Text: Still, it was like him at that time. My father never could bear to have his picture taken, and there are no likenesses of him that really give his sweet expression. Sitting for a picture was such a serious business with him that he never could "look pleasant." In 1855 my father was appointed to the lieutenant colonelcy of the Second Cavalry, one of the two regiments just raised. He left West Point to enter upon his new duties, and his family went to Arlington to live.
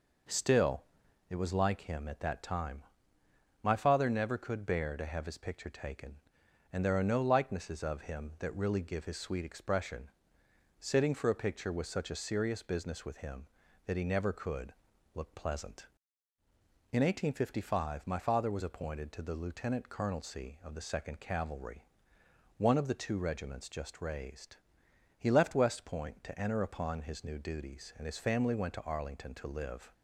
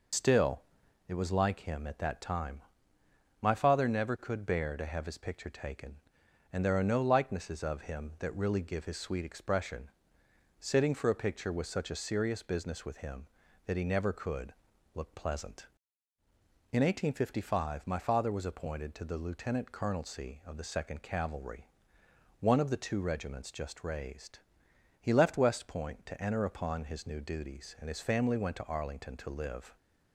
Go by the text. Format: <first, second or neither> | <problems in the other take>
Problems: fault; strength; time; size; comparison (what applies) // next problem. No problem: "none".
first | loses the start of "Still"; at 0.1 s; 70 ms // pauses between "could" and "look"; at 14.5 s; 0.42 s long; also in the first